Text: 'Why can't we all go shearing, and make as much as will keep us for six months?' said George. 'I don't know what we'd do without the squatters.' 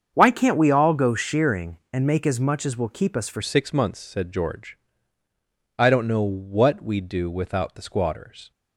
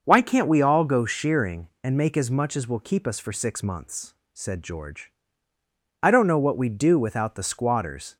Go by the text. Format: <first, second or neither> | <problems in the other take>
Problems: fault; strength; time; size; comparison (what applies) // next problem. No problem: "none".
second | starts louder than the rest; strong; until 1.1 s; 7.5 dB; also in the second // changes voice at "six"; from 3.4 s on; 5.1 s long